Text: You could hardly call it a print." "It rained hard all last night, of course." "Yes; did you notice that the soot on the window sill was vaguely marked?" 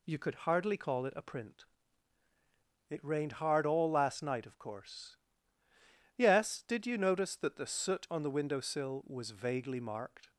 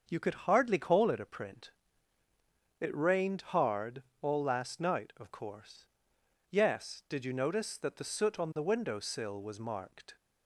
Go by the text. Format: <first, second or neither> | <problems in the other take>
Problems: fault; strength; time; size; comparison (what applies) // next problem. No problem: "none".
first | starts louder than the rest; until 1.0 s; 6.5 dB // pauses between "hard" and "all"; slight; at 4.0 s; 0.16 s long // skips "vaguely"; at 9.5 s